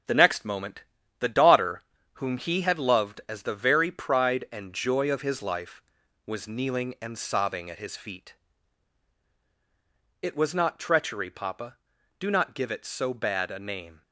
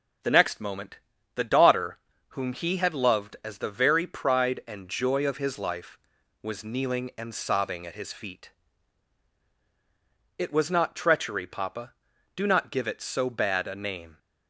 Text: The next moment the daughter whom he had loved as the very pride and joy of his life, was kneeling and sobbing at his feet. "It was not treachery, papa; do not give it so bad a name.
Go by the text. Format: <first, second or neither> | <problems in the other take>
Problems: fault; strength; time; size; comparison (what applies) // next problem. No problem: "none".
second | gets quieter; strong; throughout; 7 dB // pauses between "moment" and "the"; at 0.8 s; 0.38 s long; also in the second // pauses between "daughter" and "whom"; slight; at 1.8 s; 0.32 s long; slight in the second